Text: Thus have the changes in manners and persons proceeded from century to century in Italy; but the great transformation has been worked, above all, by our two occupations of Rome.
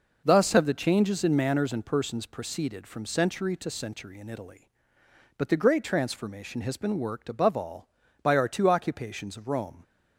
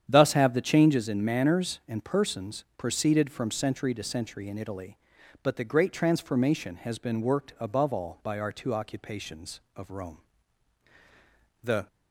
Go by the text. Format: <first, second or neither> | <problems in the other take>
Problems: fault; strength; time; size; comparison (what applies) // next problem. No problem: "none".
first | starts louder than the rest; strong; until 1.0 s; 9 dB // goes on to say "The"; slight; from 11.6 s on; 0.26 s long